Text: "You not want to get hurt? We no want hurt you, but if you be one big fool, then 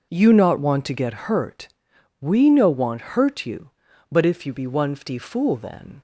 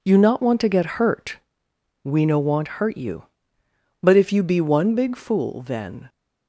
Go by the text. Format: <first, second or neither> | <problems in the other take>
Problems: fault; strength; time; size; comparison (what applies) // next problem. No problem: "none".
second | says "fty" for "big"; at 4.9 s